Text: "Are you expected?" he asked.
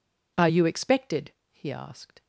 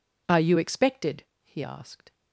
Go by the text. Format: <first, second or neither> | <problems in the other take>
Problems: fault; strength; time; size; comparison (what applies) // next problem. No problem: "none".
neither | none